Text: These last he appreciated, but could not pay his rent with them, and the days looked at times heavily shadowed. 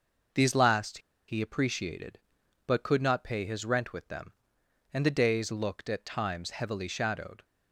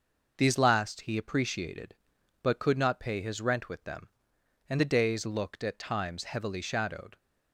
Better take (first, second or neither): second